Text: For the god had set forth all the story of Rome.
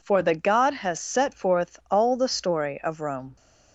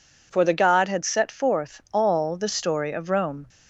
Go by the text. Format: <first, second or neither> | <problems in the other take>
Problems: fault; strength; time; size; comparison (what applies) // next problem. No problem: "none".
second | says "has" for "had"; at 0.7 s